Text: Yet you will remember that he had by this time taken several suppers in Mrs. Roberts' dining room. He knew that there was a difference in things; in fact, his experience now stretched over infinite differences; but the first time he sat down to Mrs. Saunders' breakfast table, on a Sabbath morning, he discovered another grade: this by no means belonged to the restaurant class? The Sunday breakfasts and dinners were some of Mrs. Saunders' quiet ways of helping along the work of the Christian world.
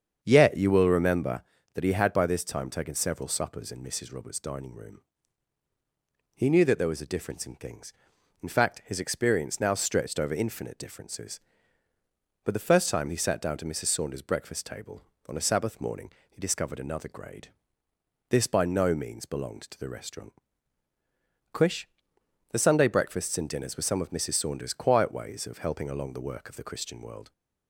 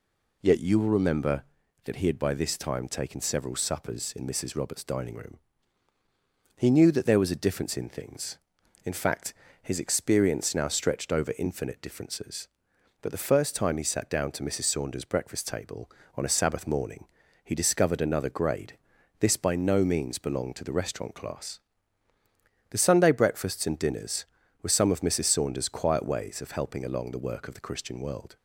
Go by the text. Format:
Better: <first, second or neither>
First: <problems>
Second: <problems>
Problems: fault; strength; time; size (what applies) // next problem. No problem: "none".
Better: second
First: starts louder than the rest; strong; until 1.2 s; 7.5 dB // says "quish" for "class"; at 21.5 s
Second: none